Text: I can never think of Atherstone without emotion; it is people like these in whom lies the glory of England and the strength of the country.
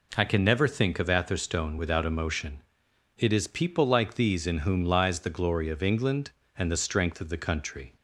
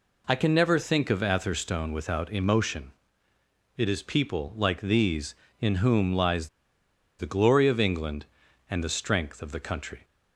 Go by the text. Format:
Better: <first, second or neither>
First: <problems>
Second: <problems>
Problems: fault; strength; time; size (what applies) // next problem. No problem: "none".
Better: first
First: none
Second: pauses between "lies" and "the"; noticeable; at 6.4 s; 0.72 s long